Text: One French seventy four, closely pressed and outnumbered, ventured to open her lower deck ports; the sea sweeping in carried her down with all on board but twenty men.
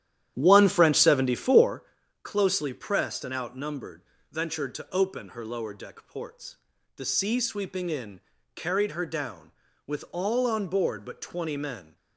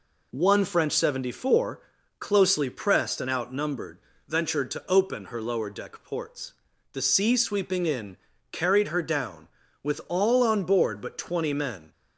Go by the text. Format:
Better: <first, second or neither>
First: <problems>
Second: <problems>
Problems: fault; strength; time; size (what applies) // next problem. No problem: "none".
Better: second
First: starts louder than the rest; strong; until 1.8 s; 11 dB // pauses between "in" and "carried"; slight; at 8.1 s; 0.34 s long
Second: pauses between "in" and "carried"; slight; at 8.1 s; 0.34 s long